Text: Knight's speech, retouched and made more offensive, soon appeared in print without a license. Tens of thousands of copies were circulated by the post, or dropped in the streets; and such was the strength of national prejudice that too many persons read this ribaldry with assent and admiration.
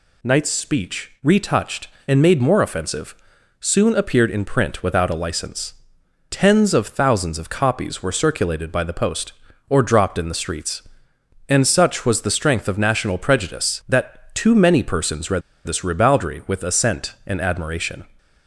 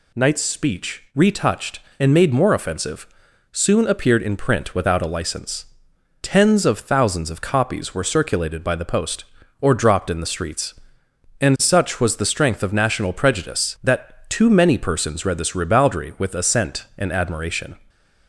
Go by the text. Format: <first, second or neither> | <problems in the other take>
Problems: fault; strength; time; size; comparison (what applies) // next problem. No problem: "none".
second | pauses between "read" and "this"; slight; at 15.4 s; 0.24 s long